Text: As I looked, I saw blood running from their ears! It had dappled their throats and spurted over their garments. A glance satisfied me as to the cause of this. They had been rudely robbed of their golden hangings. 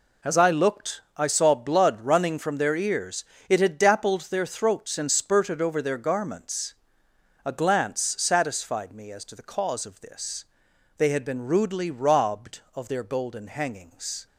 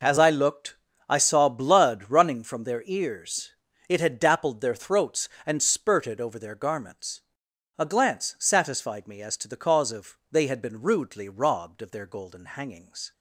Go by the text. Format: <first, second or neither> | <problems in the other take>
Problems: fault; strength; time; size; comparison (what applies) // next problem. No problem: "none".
first | skips "this"; at 10.2 s